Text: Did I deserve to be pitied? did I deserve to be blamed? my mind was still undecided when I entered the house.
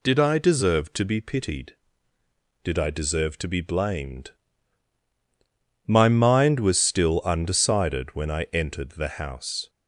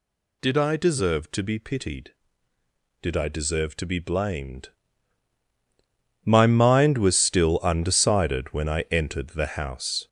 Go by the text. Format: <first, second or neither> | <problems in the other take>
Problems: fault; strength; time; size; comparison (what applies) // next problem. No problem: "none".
first | gets louder; noticeable; throughout; 5 dB